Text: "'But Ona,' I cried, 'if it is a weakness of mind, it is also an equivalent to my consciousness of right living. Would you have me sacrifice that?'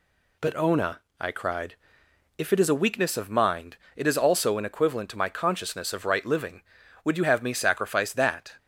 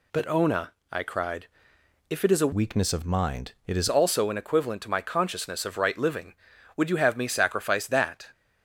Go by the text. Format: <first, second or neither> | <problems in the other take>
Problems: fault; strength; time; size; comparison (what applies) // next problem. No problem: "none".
first | changes voice from "weakness" to "is"; from 2.5 to 3.8 s; 1.3 s long